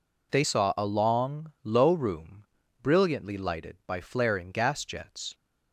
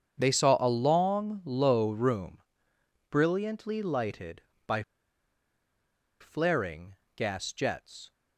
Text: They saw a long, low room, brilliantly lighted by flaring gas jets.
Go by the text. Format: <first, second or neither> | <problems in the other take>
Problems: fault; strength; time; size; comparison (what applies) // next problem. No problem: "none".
first | starts louder than the rest; strong; until 1.2 s; 7.5 dB // pauses between "by" and "flaring"; strong; at 4.8 s; 1.3 s long // pauses between "flaring" and "gas"; slight; at 6.9 s; 0.20 s long